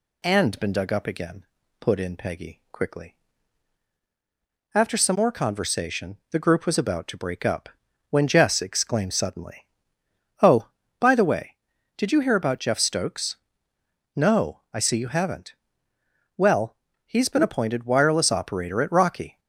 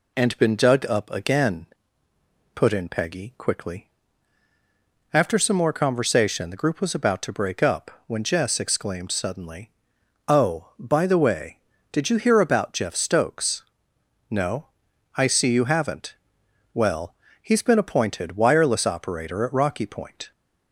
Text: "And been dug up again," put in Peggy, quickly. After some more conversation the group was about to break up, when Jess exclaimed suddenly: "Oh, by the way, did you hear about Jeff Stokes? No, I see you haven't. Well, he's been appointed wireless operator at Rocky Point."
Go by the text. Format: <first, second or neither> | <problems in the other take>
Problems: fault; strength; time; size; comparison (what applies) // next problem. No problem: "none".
second | stops before "Point"; at 19.3 s